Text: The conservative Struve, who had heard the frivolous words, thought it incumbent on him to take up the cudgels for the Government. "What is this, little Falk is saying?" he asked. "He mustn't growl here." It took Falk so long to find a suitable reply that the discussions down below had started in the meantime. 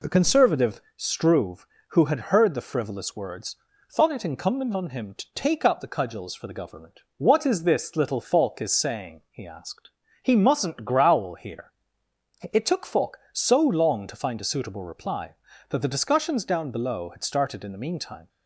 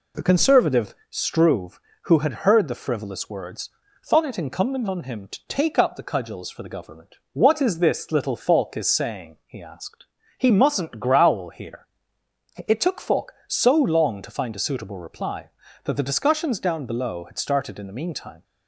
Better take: neither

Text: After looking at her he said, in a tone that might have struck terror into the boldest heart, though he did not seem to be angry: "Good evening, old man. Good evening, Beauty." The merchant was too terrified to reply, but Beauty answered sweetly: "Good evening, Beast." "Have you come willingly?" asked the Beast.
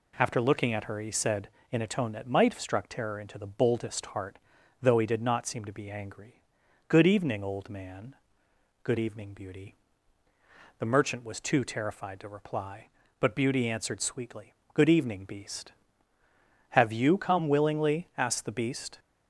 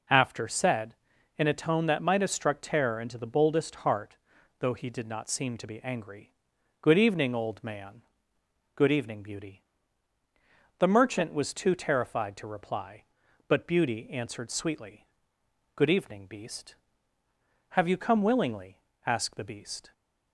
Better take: first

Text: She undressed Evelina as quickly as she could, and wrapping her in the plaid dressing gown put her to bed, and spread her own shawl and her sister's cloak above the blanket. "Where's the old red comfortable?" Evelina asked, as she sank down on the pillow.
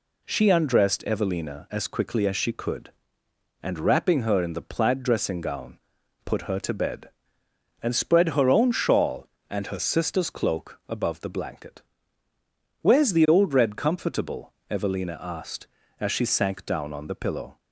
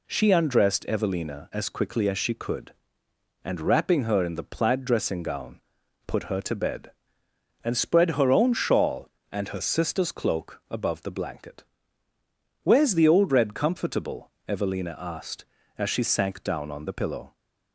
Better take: neither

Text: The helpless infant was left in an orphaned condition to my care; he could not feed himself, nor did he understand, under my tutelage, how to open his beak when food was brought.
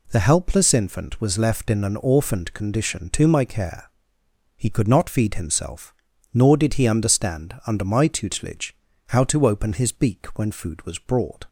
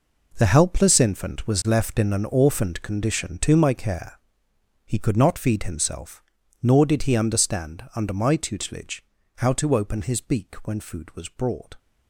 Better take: first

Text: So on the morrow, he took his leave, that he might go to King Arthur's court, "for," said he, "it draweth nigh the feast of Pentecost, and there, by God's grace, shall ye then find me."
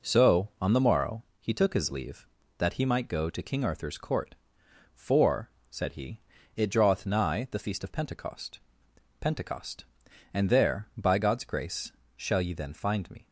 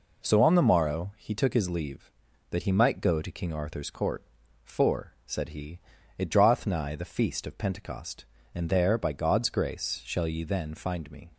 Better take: second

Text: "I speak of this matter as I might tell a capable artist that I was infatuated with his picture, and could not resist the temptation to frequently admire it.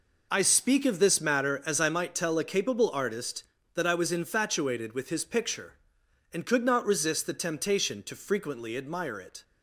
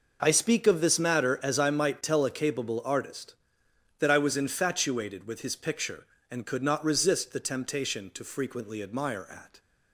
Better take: first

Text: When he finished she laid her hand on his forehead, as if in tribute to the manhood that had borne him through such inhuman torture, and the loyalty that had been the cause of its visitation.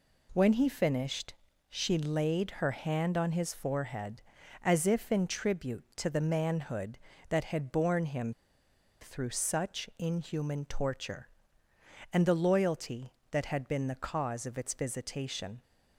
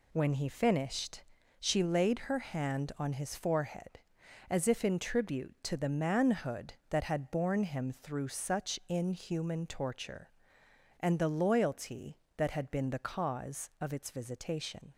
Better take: second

